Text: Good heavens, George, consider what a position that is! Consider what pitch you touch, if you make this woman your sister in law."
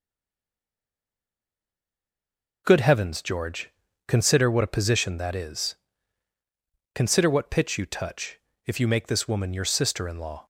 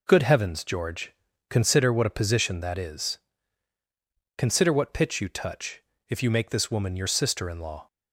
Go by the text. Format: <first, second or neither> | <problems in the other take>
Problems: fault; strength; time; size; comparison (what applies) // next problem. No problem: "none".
second | stays silent before the first word; strong; until 2.6 s; 2.6 s long